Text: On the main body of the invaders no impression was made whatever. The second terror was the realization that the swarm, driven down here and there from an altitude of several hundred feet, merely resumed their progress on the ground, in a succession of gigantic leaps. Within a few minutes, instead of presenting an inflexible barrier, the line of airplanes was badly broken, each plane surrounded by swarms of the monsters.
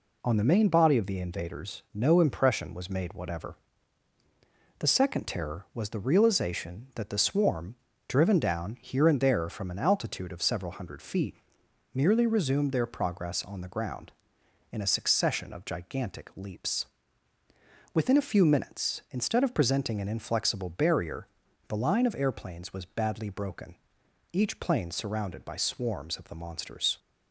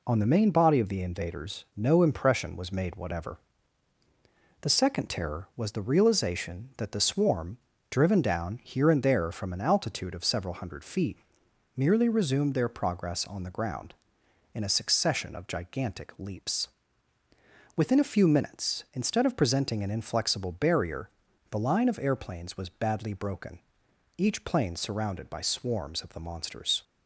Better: neither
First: none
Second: none

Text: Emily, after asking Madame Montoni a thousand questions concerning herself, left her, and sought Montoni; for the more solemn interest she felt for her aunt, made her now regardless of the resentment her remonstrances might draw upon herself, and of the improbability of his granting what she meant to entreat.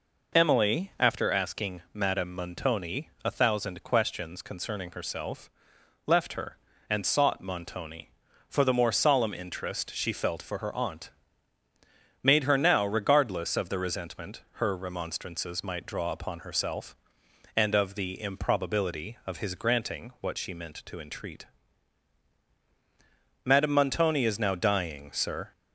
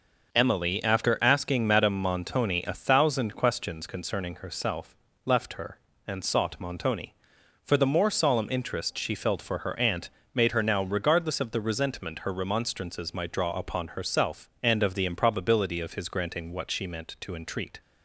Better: second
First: goes on to say "Madame Montoni is now dying sir"; strong; from 23.4 s on; 2.0 s long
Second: none

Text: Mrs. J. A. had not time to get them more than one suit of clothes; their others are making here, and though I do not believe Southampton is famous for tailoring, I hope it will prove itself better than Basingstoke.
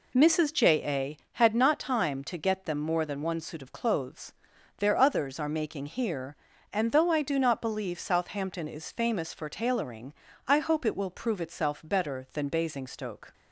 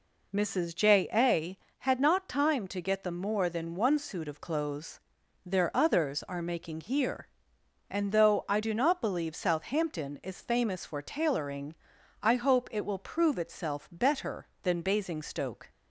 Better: neither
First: none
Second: none

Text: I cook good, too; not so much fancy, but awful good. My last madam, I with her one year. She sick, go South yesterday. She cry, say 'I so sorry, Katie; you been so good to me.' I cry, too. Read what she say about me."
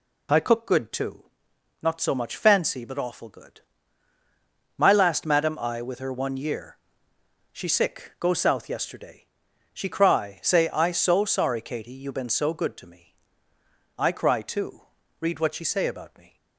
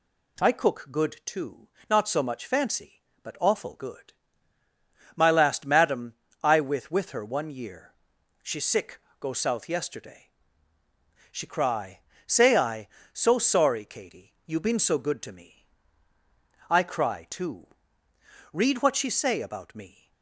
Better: first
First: none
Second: says "with" twice; at 6.9 s

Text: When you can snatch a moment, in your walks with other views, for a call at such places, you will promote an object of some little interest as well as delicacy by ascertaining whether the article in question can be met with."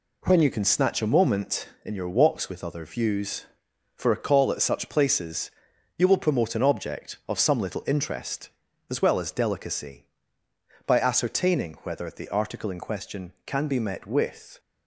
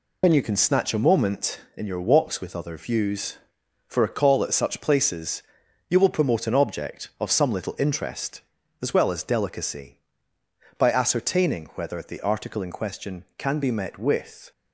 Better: first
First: none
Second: loses the start of "When"; at 0.2 s; 85 ms

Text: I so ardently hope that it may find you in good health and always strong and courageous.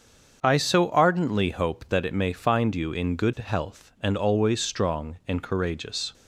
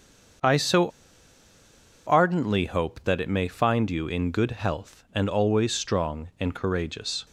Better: first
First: starts louder than the rest; until 1.4 s; 7 dB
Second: starts louder than the rest; until 2.5 s; 7 dB // pauses between "so" and "ardently"; at 0.8 s; 1.1 s long

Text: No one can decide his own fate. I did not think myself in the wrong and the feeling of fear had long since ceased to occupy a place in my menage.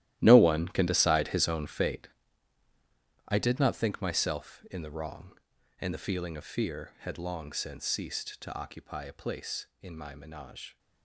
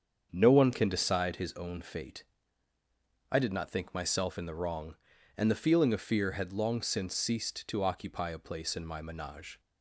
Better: second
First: gets quieter; strong; throughout; 14 dB // starts louder than the rest; strong; until 1.2 s; 14 dB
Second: starts louder than the rest; strong; until 1.3 s; 7.5 dB

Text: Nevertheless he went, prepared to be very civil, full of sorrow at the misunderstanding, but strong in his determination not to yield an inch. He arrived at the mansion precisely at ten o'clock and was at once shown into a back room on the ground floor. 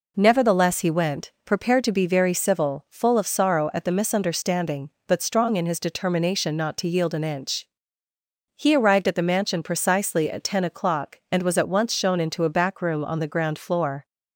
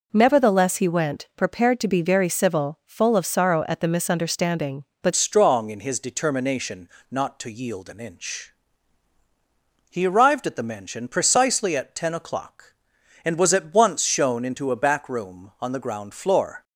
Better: first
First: none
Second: changes voice at "strong"; from 5.1 s on; 11.5 s long // pauses between "determination" and "not"; slight; at 6.8 s; 0.22 s long

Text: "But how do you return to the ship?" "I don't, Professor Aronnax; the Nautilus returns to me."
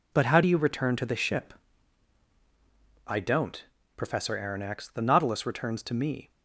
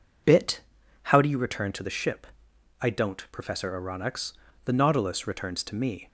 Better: first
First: none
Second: says "Bit" for "But"; at 0.2 s

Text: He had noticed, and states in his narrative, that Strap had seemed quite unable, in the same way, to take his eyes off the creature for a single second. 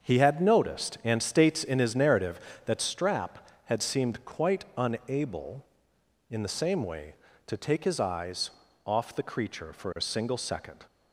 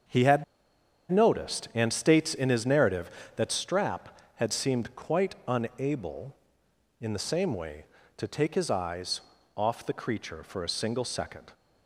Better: first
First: starts louder than the rest; until 1.0 s; 7 dB // pauses between "eyes" and "off"; slight; at 8.4 s; 0.34 s long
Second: starts louder than the rest; until 1.8 s; 7 dB // pauses between "had" and "noticed"; noticeable; at 0.4 s; 0.67 s long // pauses between "eyes" and "off"; slight; at 9.1 s; 0.34 s long

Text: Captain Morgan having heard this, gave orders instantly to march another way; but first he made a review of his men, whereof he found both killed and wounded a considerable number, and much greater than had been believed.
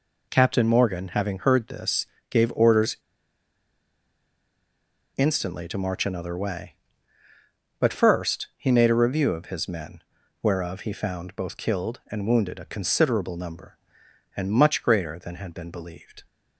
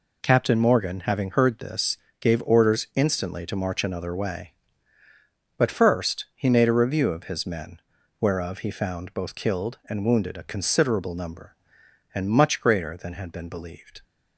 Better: second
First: pauses between "orders" and "instantly"; strong; at 2.9 s; 2.1 s long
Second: none

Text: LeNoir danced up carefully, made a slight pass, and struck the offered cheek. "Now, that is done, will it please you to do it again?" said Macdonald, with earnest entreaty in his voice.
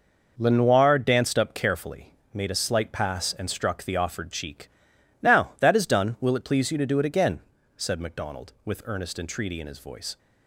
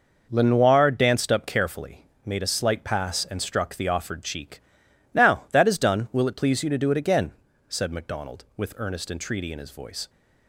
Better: neither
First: none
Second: none

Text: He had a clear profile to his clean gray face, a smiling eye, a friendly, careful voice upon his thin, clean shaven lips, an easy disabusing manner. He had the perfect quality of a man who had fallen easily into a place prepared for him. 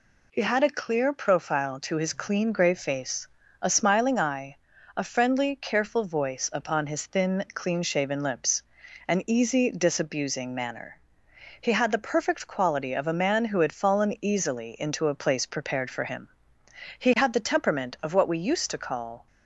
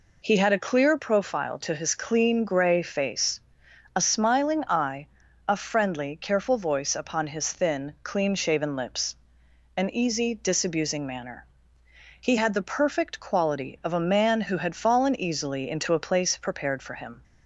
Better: second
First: goes on to say "He had the temperament of what we used to call"; strong; from 16.9 s on; 2.2 s long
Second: none

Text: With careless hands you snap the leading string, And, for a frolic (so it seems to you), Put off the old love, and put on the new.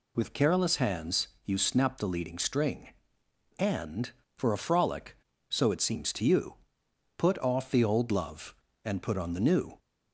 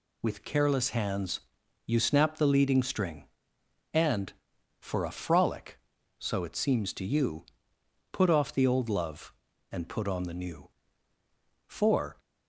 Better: first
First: pauses between "hands" and "you"; slight; at 1.2 s; 0.16 s long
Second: pauses between "hands" and "you"; noticeable; at 1.3 s; 0.46 s long // goes on to say "For"; from 11.6 s on; 0.52 s long

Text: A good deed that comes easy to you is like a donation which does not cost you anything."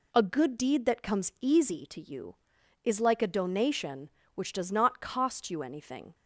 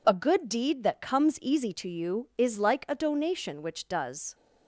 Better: first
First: none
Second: stops before "not cost you anything"; at 4.3 s

